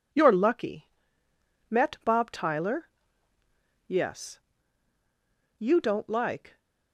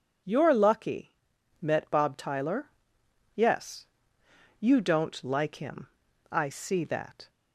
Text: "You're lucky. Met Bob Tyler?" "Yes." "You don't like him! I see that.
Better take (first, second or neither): second